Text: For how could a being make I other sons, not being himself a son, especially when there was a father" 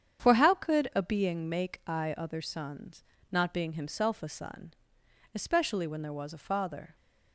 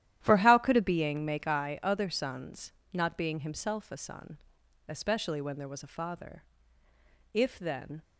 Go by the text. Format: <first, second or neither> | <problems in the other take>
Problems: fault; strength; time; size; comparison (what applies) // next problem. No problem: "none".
first | starts louder than the rest; strong; until 1.2 s; 12 dB; strong in the first // goes on to say "If then"; noticeable; from 7.3 s on; 0.68 s long